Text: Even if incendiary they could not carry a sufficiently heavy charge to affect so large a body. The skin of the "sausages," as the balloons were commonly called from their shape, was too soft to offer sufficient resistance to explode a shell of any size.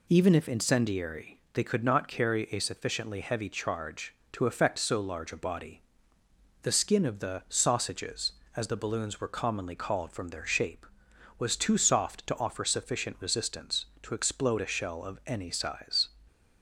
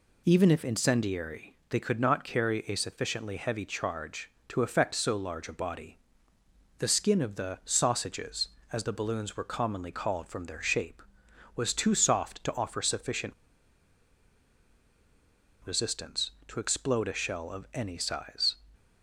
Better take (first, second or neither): first